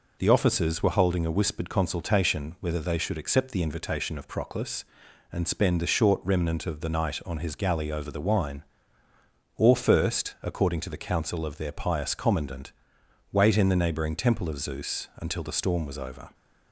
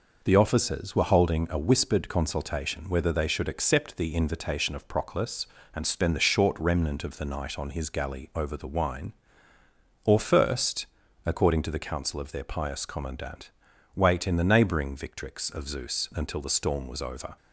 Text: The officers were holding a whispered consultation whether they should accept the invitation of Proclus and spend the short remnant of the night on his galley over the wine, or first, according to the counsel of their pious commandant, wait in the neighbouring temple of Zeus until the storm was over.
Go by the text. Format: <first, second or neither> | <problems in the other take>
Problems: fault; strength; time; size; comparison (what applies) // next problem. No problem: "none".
first | says "victrix" for "temple"; at 14.9 s